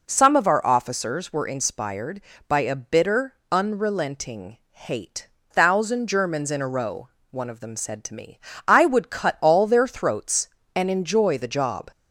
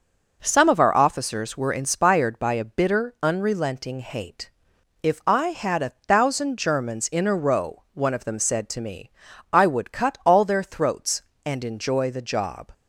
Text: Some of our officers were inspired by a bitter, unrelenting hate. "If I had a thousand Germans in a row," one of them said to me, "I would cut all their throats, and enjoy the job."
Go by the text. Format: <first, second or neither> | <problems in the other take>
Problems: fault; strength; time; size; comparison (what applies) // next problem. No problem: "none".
second | skips "If I had a"; at 5.3 s